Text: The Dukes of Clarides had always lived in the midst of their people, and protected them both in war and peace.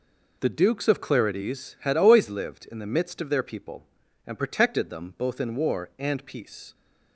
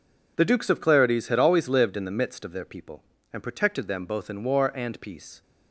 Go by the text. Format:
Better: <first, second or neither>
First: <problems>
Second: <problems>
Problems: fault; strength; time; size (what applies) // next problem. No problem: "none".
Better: neither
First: none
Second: none